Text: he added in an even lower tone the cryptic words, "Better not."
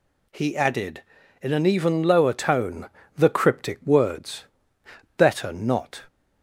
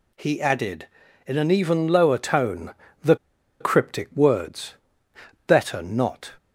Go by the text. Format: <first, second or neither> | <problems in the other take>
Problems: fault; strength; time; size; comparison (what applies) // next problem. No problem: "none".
first | pauses between "tone" and "the"; slight; at 2.7 s; 0.28 s long; slight in the first // pauses between "the" and "cryptic"; at 3.1 s; 0.45 s long